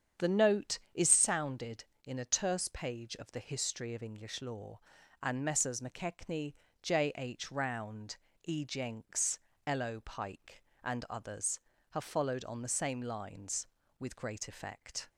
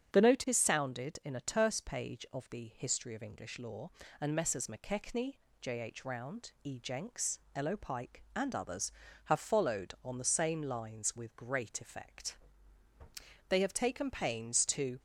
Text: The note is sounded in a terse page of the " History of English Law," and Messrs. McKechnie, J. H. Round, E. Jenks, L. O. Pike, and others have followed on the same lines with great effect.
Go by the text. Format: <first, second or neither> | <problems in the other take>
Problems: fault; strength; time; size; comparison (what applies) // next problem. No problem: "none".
first | starts louder than the rest; strong; until 1.1 s; 7.5 dB; strong in the first // goes on to say "They have taken pains to"; from 13.4 s on; 1.5 s long